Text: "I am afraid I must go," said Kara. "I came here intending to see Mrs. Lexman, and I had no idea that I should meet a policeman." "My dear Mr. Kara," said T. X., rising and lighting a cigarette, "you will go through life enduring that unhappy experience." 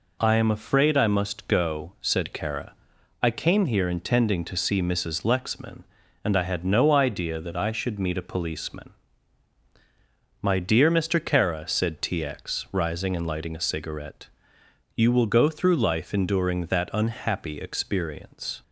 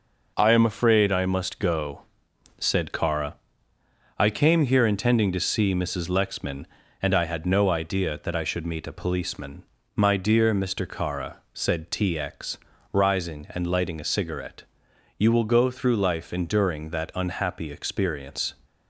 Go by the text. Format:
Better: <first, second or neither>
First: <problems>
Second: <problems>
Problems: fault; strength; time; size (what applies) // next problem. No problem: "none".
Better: neither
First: none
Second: none